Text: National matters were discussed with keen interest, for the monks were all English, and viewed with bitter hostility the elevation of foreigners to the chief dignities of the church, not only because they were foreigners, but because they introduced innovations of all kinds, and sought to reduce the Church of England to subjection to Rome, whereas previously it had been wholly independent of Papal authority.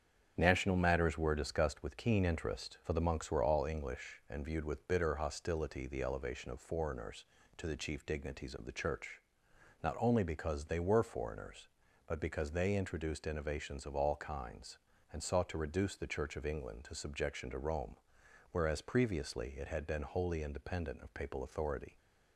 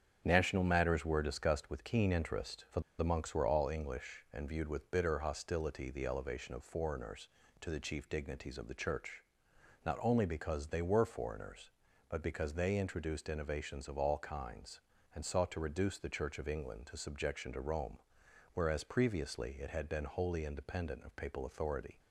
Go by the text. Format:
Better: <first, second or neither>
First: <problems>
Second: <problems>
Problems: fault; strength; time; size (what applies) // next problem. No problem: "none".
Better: first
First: starts louder than the rest; strong; until 1.3 s; 8 dB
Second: starts louder than the rest; strong; until 1.2 s; 8 dB // pauses between "for" and "the"; slight; at 2.8 s; 0.18 s long